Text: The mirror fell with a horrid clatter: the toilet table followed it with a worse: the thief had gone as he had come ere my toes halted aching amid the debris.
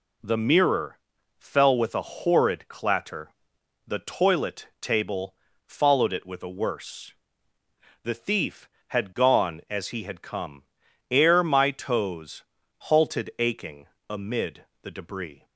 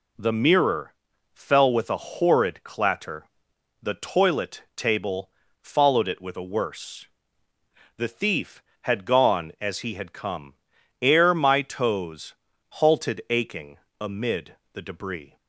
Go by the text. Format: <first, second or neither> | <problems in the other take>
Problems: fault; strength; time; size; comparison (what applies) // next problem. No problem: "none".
neither | pauses between "mirror" and "fell"; the same in both // pauses between "table" and "followed"; slight; the same in both // pauses between "come" and "ere"; noticeable; the same in both // pauses between "toes" and "halted"; the same in both // pauses between "aching" and "amid"; slight; the same in both // pauses between "amid" and "the"; slight; the same in both